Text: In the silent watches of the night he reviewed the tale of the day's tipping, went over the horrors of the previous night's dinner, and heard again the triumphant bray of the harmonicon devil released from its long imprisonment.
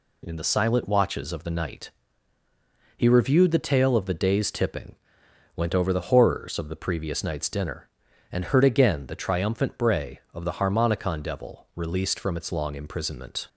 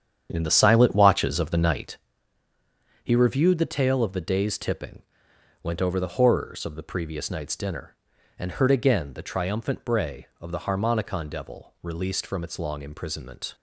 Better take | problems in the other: first | starts louder than the rest; strong; until 1.9 s; 8.5 dB // pauses between "night" and "he"; at 1.9 s; 1.0 s long; also in the first

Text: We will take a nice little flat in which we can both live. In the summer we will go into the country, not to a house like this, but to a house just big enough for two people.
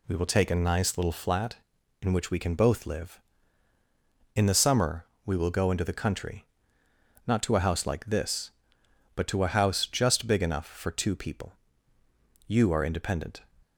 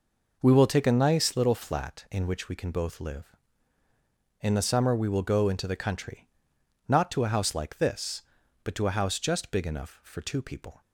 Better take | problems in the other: second | pauses between "summer" and "we"; slight; at 5.0 s; 0.18 s long // goes on to say "You are independent"; noticeable; from 12.4 s on; 0.98 s long

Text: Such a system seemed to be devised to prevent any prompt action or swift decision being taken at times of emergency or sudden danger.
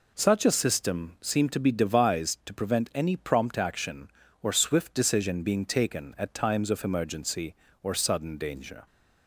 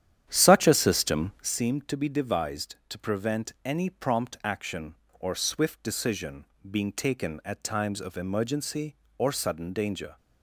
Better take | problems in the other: first | starts louder than the rest; strong; until 1.6 s; 10 dB // pauses between "decision" and "being"; slight; at 6.4 s; 0.22 s long

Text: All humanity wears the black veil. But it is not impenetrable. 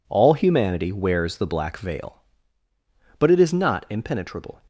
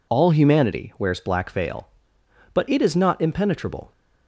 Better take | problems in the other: first | skips "the"; at 1.1 s

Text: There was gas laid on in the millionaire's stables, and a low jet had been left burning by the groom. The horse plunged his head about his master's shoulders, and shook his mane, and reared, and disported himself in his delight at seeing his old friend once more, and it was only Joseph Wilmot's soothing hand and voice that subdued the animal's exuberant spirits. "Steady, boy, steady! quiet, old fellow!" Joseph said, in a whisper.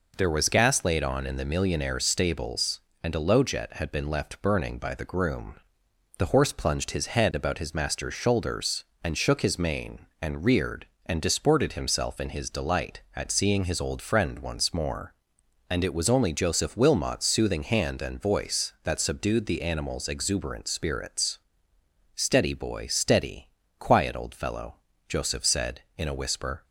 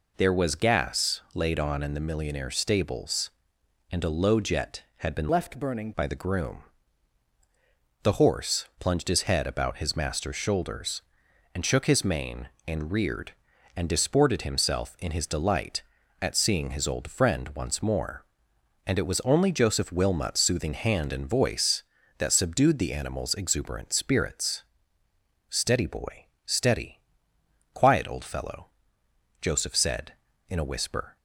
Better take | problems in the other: first | changes voice from "left" to "burning"; from 5.2 to 5.9 s; 0.7 s long

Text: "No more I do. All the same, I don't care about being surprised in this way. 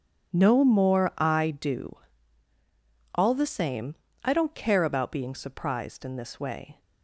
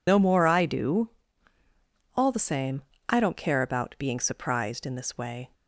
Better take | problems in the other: first | loses the start of "No"; at 0.0 s; 70 ms

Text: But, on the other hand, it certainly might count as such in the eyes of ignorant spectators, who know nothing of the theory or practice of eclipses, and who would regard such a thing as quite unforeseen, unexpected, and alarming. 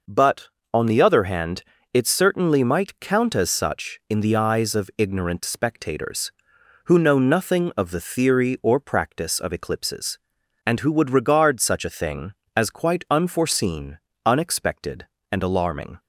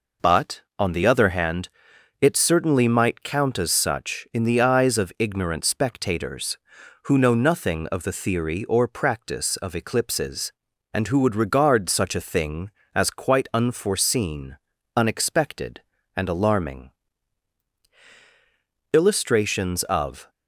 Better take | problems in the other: first | goes on to say "Illustrations of"; from 18.9 s on; 1.3 s long

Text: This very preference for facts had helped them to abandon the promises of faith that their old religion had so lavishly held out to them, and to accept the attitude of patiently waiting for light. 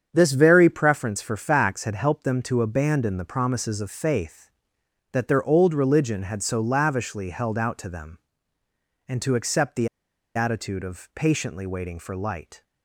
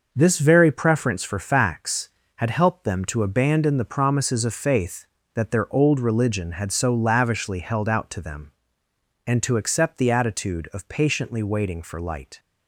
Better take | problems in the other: second | starts louder than the rest; strong; until 1.1 s; 7.5 dB // pauses between "the" and "attitude"; noticeable; at 9.8 s; 0.47 s long

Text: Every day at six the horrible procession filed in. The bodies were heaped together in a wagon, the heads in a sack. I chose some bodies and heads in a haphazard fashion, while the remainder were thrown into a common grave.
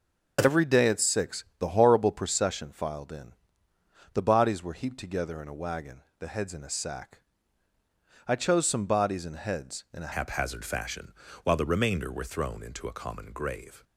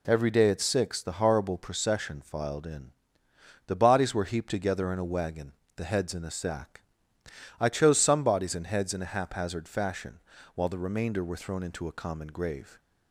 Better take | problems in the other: second | changes voice at "haphazard"; from 10.1 s on; 3.7 s long

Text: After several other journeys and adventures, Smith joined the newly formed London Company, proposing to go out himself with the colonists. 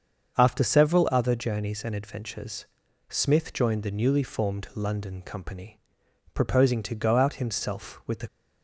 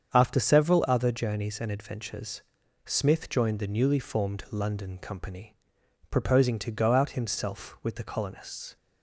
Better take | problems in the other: second | starts louder than the rest; until 1.4 s; 7 dB; strong in the second // stops before "colonists"; at 8.2 s

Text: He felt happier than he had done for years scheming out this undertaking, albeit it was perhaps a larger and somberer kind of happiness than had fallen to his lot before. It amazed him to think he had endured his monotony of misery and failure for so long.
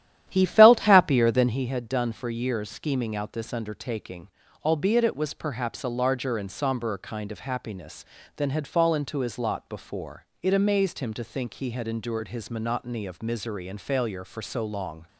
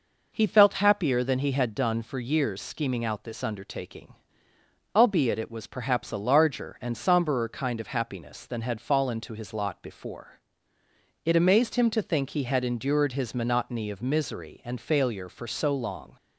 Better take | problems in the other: second | starts louder than the rest; strong; until 1.6 s; 11.5 dB

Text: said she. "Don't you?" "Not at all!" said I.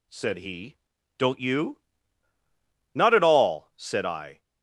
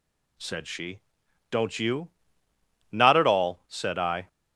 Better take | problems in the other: second | says "he" for "she"; at 0.3 s

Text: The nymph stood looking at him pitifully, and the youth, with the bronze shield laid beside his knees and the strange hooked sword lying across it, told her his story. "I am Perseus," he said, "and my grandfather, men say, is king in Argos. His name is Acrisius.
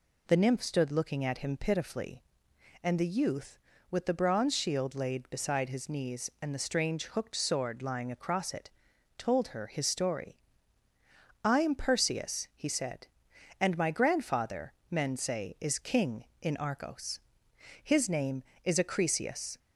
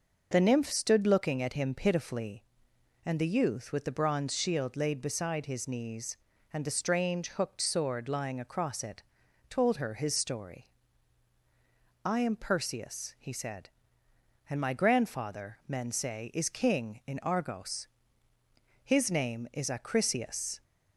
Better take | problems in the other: neither | none

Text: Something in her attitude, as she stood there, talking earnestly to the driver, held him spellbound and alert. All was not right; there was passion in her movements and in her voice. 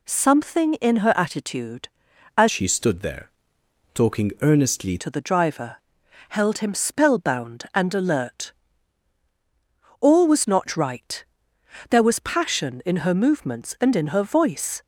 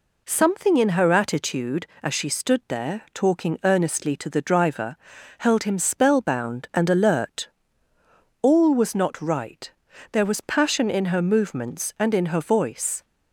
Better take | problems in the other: second | changes voice from "she" to "earnestly"; from 2.4 to 4.9 s; 2.5 s long

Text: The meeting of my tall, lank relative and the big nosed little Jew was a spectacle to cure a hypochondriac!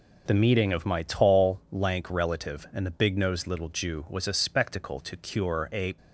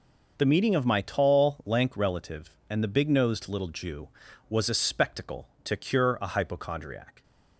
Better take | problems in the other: second | stops before "hypochondriac"; at 5.9 s

